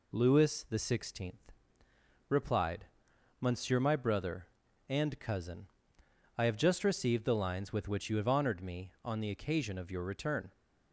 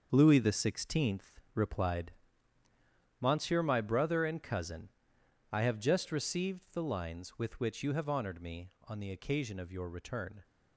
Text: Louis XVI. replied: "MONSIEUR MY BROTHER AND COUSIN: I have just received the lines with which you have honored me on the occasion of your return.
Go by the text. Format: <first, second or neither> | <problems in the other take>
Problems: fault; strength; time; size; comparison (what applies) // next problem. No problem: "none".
first | gets quieter; strong; throughout; 9 dB